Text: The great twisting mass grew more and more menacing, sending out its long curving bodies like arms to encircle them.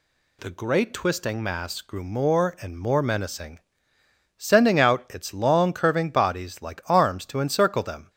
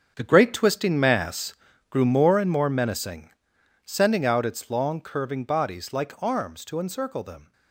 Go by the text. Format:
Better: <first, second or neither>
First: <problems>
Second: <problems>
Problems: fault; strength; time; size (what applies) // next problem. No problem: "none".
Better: first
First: none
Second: gets quieter; strong; throughout; 12 dB // pauses between "mass" and "grew"; slight; at 1.5 s; 0.34 s long